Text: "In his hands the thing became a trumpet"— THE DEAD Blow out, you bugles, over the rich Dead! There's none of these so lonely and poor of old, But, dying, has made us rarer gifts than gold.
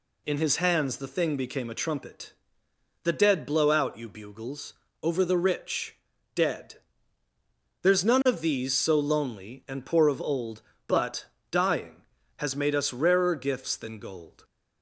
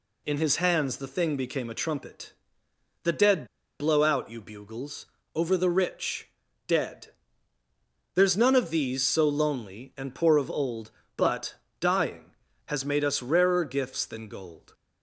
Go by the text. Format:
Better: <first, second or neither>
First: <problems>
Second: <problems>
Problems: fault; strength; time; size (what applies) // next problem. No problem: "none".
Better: first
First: pauses between "rich" and "Dead"; slight; at 5.9 s; 0.36 s long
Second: pauses between "DEAD" and "Blow"; slight; at 3.4 s; 0.34 s long // pauses between "rich" and "Dead"; slight; at 6.2 s; 0.36 s long